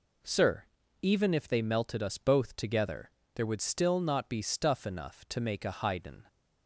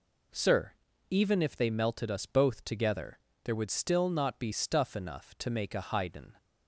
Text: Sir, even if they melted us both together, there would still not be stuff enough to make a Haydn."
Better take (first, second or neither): neither